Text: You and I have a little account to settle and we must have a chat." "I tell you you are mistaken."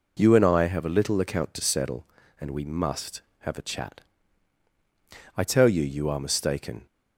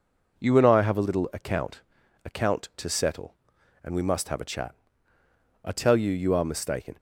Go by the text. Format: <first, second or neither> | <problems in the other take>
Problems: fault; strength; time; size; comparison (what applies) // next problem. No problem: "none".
first | says "account" twice; at 2.2 s